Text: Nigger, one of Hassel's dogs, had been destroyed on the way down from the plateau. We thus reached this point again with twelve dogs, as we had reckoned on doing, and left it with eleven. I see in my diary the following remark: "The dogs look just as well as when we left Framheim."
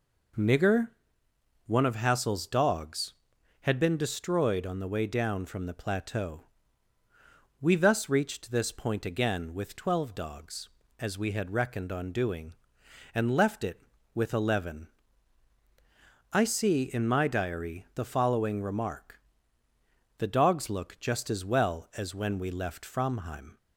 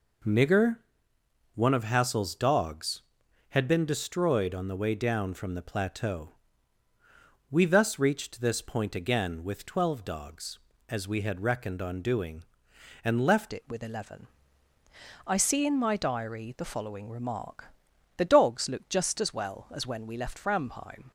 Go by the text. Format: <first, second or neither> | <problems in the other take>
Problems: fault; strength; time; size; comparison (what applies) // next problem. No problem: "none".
first | changes voice at "it"; from 13.5 s on; 7.6 s long